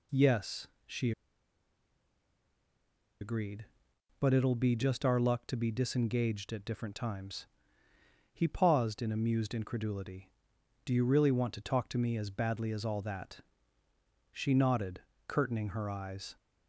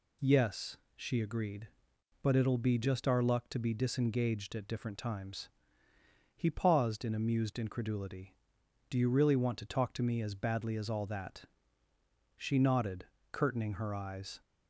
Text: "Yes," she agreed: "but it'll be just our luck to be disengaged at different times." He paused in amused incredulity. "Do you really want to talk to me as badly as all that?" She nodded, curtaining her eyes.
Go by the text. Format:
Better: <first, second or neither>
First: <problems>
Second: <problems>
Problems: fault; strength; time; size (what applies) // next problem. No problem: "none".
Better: second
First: pauses between "she" and "agreed"; strong; at 1.1 s; 2.0 s long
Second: none